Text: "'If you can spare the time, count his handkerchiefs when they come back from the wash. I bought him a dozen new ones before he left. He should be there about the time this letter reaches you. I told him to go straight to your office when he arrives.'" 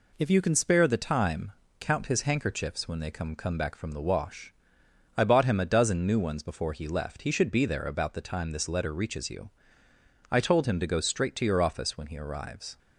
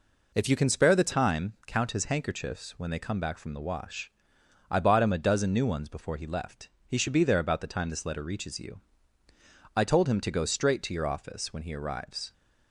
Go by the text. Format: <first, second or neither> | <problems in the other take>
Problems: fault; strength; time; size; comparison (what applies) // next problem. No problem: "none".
second | says "come" twice; at 3.3 s